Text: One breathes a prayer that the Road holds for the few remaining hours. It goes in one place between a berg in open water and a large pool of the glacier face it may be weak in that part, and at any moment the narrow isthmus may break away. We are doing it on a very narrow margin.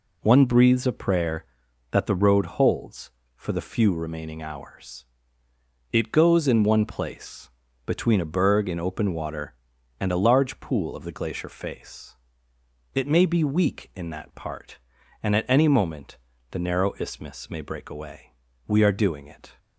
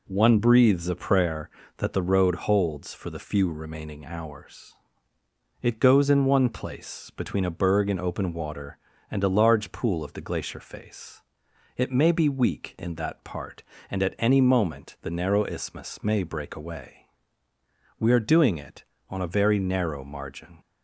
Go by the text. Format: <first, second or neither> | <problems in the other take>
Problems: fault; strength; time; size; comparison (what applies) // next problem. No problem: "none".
second | pauses between "place" and "between"; slight; at 7.4 s; 0.36 s long // pauses between "face" and "it"; noticeable; at 12.1 s; 0.78 s long; noticeable in the second // pauses between "moment" and "the"; slight; at 16.1 s; 0.34 s long // stops before "on a very narrow margin"; at 19.5 s